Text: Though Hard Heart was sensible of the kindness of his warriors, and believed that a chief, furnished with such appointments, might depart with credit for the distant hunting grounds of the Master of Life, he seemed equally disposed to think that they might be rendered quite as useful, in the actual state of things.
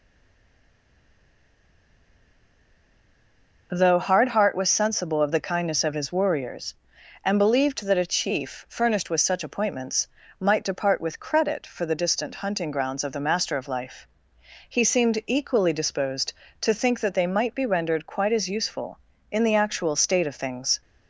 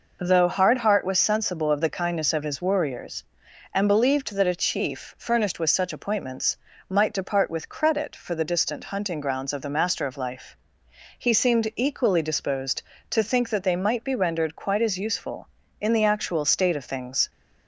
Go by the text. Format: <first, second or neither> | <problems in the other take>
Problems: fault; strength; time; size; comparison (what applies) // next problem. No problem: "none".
second | stays silent before the first word; strong; until 3.6 s; 3.6 s long